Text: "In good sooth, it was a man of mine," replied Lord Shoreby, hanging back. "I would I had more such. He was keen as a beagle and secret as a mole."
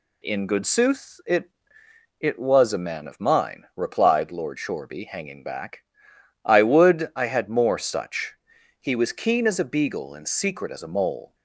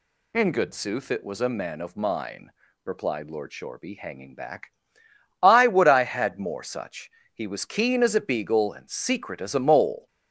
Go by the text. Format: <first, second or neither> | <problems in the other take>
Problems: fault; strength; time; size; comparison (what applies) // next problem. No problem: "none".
second | says "it" twice; at 2.2 s